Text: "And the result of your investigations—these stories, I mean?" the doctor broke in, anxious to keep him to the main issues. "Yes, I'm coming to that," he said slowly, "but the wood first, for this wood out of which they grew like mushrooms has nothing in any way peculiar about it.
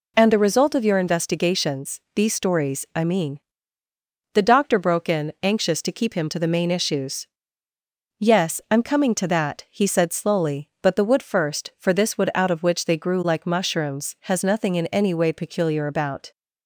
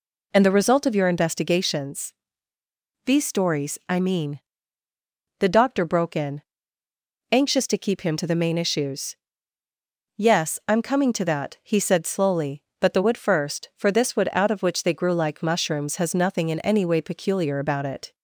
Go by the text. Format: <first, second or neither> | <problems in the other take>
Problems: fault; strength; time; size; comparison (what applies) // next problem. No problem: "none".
second | stops before "it"; at 16.3 s